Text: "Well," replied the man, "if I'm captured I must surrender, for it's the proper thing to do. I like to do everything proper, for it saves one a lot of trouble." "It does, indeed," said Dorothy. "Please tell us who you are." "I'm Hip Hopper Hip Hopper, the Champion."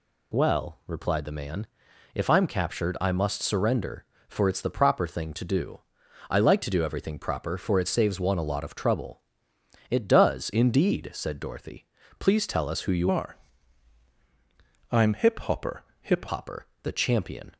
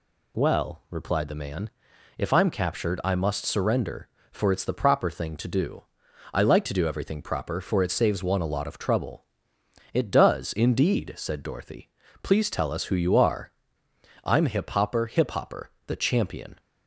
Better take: second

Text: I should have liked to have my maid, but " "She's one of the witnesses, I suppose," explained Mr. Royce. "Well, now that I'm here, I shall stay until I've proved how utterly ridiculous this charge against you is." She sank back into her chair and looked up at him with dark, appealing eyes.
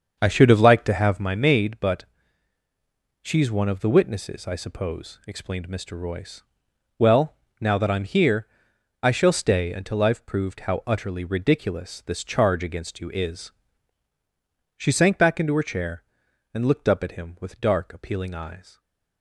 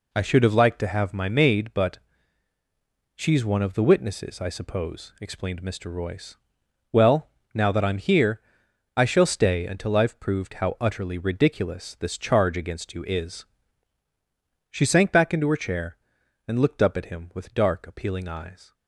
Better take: second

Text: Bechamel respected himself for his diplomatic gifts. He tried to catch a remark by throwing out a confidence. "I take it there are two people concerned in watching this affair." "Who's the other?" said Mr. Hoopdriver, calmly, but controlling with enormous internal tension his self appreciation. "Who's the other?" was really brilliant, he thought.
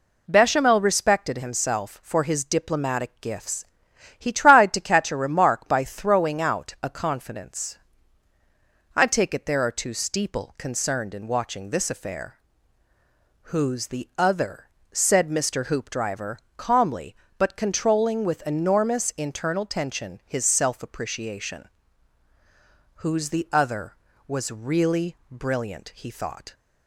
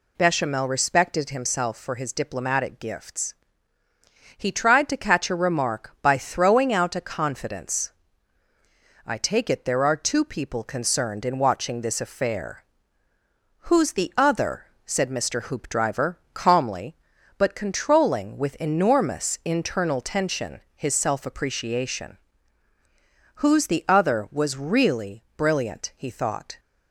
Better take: second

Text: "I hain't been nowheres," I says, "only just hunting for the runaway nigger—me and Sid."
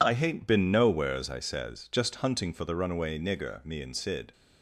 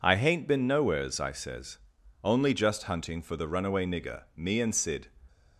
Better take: second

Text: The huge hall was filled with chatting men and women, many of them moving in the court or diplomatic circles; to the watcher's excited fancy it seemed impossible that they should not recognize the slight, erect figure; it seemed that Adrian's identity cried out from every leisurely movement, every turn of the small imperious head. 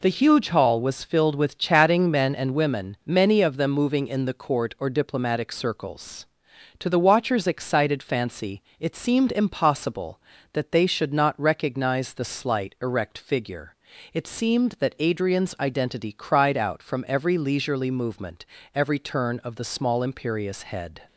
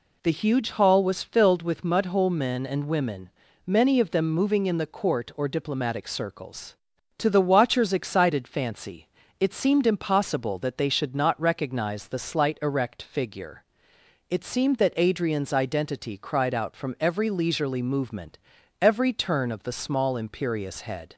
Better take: first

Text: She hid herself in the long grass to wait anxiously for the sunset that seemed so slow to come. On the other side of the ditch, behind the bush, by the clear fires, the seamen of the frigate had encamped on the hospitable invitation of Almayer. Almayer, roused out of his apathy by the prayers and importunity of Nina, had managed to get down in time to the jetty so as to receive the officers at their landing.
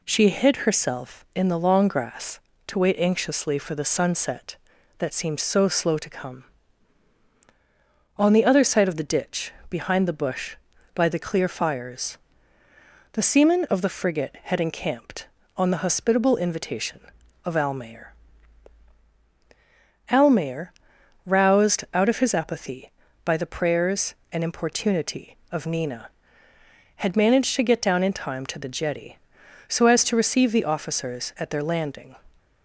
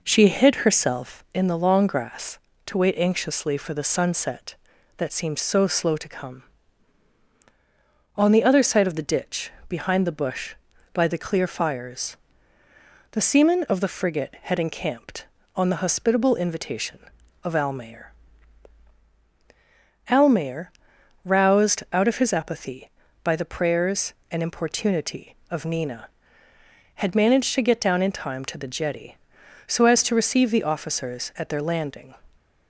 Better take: first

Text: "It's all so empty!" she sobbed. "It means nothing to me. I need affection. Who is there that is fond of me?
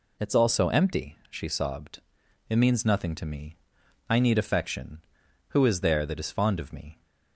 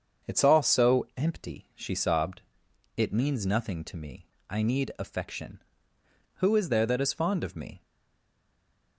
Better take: first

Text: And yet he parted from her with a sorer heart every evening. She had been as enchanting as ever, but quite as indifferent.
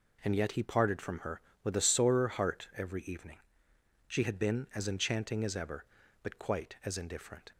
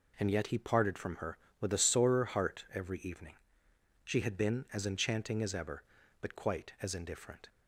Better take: neither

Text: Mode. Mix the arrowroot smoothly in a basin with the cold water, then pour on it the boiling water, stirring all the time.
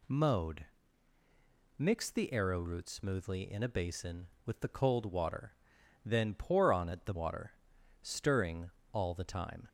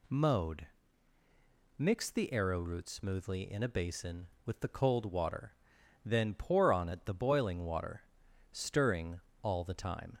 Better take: second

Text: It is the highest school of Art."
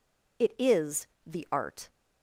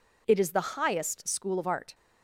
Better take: second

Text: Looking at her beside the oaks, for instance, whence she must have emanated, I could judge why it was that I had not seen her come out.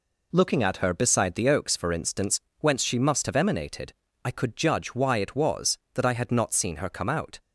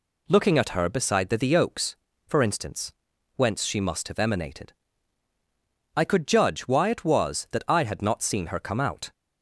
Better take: first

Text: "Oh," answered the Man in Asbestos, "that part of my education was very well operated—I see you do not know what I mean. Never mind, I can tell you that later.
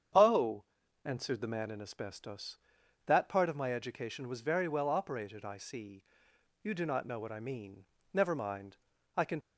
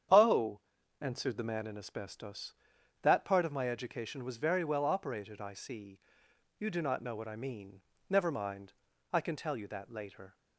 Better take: second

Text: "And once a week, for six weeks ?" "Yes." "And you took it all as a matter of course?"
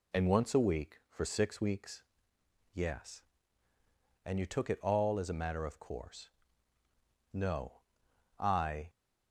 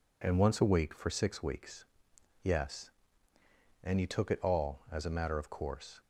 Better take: second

